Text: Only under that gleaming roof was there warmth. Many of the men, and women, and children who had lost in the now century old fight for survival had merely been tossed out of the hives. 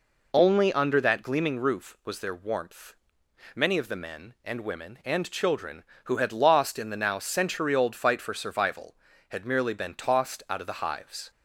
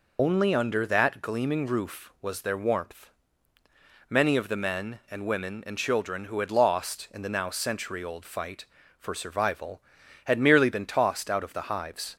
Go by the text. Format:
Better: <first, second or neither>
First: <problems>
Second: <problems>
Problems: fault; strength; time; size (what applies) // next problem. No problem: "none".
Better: first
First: none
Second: loses the start of "Only"; at 0.1 s; 80 ms